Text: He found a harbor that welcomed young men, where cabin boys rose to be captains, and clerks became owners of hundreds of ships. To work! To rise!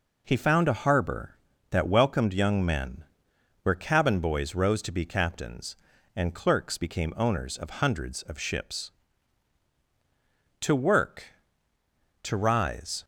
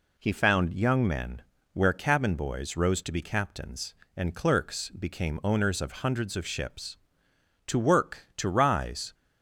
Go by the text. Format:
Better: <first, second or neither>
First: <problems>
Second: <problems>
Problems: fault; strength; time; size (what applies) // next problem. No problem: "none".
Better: first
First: none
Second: skips "a harbor that welcomed"; at 0.7 s